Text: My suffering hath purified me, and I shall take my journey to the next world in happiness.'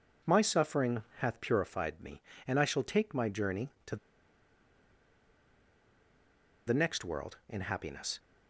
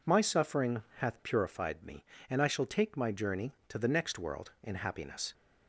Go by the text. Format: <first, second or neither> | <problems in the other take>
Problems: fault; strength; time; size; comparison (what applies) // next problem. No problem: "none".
second | pauses between "to" and "the"; strong; at 3.9 s; 2.7 s long